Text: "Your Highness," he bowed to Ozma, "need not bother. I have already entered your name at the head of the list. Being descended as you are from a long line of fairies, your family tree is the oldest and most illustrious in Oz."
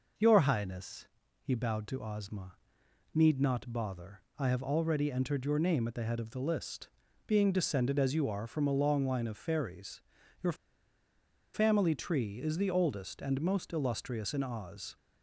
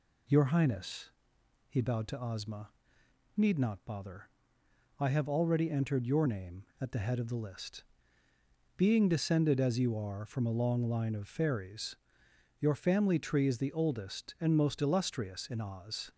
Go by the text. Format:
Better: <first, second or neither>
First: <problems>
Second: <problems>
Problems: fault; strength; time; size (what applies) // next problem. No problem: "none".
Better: second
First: pauses between "your" and "family"; at 10.5 s; 0.99 s long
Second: none